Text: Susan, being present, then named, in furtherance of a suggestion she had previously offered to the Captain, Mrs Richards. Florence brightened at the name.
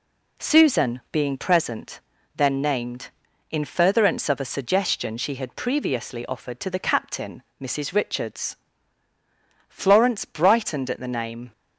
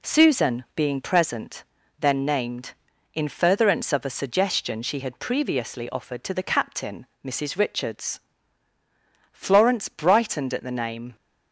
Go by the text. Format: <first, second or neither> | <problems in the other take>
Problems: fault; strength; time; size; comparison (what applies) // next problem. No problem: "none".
neither | none